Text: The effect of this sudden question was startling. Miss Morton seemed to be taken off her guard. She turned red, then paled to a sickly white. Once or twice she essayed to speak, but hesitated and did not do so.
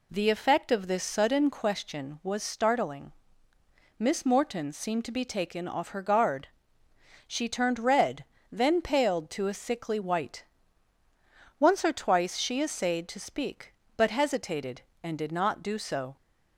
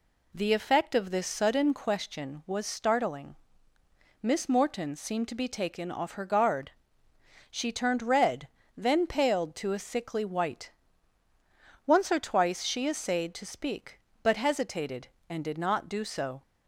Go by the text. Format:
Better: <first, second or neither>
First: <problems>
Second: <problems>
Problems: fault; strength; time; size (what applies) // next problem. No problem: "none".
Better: neither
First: none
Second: none